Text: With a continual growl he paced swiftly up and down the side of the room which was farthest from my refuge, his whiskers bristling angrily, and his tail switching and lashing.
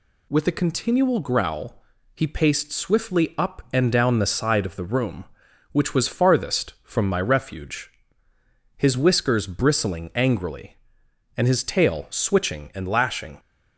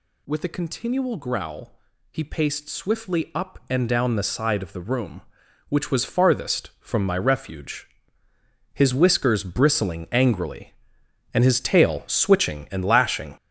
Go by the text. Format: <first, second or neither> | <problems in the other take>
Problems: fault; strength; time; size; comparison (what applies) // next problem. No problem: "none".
first | gets louder; strong; throughout; 8 dB // pauses between "growl" and "he"; slight; at 1.7 s; 0.34 s long; slight in the first